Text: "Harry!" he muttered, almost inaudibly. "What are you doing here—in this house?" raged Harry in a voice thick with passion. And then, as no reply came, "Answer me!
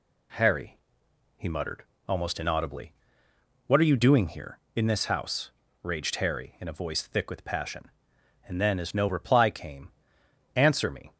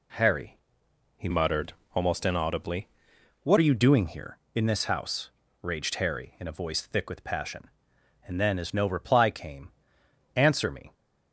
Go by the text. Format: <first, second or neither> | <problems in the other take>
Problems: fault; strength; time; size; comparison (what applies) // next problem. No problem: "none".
first | changes voice from "muttered" to "What"; from 1.3 to 3.5 s; 2.2 s long